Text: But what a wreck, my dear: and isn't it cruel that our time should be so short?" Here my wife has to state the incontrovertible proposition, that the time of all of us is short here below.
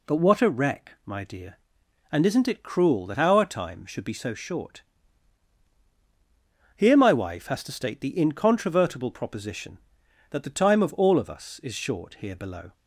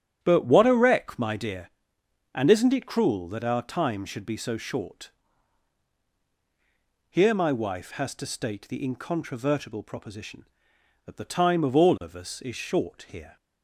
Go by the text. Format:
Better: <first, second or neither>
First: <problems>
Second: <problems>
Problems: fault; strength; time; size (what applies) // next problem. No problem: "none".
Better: first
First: none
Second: starts louder than the rest; strong; until 1.2 s; 9.5 dB // stops before "below"; at 13.3 s